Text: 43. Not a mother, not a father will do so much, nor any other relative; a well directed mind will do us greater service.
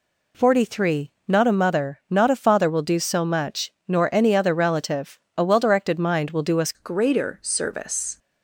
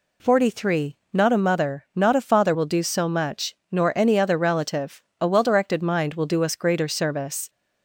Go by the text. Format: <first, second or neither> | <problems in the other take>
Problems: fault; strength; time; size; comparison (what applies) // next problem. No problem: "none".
second | changes voice at "greater"; from 6.7 s on; 1.4 s long